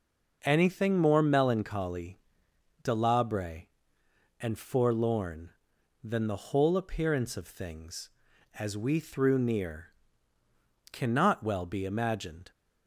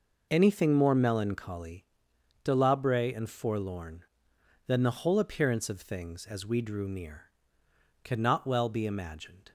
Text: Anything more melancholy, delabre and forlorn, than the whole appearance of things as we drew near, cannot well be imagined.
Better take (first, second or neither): second